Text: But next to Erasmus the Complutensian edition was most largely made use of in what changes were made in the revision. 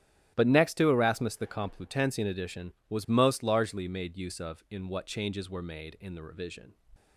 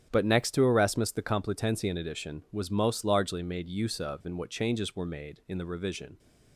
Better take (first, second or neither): neither